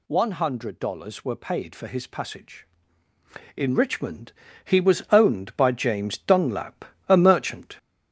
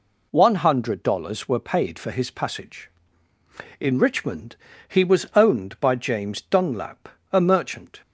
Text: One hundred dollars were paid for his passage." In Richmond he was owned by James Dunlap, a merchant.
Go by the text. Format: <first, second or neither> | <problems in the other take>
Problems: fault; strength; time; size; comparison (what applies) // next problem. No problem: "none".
second | gets louder; noticeable; throughout; 4 dB // pauses between "Richmond" and "he"; slight; at 4.3 s; 0.32 s long; slight in the second